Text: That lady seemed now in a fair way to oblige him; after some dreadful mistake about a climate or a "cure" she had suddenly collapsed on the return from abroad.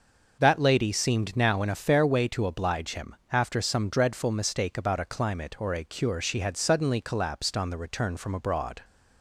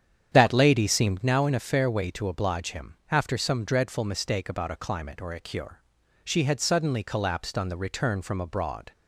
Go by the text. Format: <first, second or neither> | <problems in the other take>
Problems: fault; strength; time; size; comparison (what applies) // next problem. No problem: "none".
first | starts louder than the rest; strong; until 1.3 s; 9 dB // pauses between "cure" and "she"; at 5.8 s; 0.42 s long